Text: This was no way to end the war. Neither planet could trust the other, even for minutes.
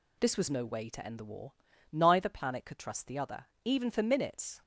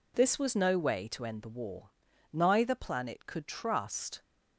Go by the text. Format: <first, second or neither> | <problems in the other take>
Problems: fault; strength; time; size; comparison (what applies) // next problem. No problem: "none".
first | stops before "the other even for minutes"; at 4.2 s